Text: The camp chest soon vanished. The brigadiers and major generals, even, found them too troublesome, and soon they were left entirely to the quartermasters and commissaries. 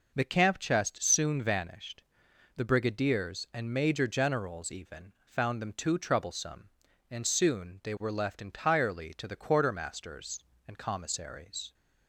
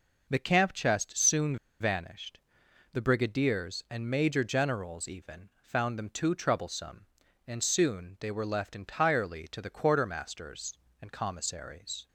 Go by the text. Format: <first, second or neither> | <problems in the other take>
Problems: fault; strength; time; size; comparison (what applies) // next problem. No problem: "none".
first | pauses between "soon" and "vanished"; slight; at 1.5 s; 0.25 s long